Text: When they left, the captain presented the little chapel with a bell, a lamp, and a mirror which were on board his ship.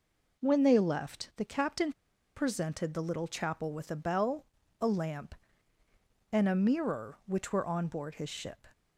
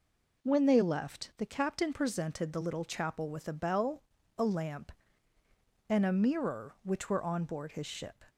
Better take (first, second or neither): second